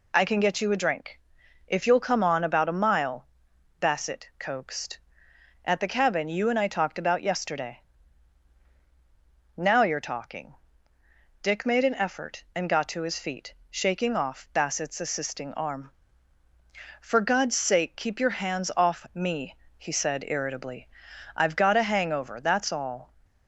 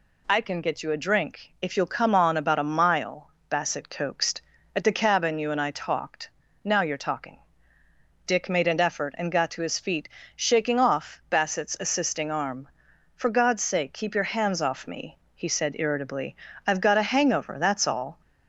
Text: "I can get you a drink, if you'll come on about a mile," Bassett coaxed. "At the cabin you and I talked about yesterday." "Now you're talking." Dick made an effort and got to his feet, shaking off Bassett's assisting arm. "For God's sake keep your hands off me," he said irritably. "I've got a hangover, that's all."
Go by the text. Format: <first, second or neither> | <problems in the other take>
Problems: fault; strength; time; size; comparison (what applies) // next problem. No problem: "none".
first | skips "about yesterday"; at 6.4 s